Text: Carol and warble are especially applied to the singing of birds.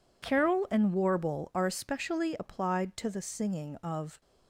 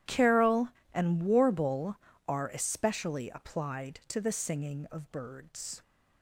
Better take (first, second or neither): second